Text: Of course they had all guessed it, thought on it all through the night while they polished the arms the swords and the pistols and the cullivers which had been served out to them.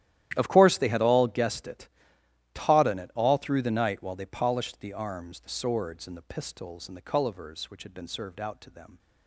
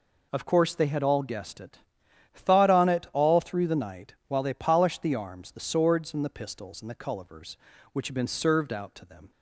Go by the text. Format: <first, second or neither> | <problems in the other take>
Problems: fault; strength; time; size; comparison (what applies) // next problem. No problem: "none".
second | starts louder than the rest; strong; until 1.3 s; 12.5 dB // says "taught" for "thought"; at 2.5 s